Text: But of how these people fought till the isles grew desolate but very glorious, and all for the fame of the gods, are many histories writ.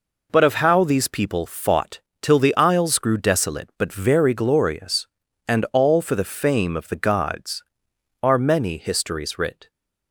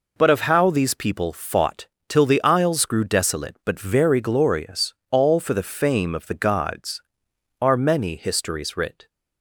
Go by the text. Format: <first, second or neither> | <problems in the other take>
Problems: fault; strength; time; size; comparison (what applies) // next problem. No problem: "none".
first | pauses between "fought" and "till"; slight; at 1.8 s; 0.22 s long; slight in the first // skips "and"; at 5.0 s